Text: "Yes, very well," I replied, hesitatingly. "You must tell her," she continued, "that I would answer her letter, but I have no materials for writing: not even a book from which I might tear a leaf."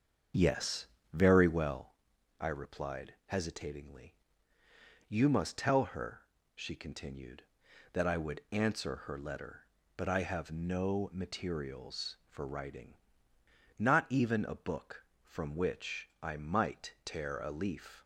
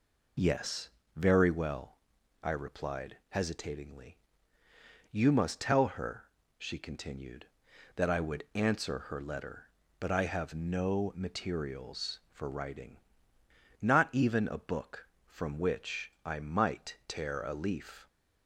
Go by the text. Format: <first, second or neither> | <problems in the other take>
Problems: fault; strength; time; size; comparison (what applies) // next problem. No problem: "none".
second | starts louder than the rest; until 1.9 s; 7 dB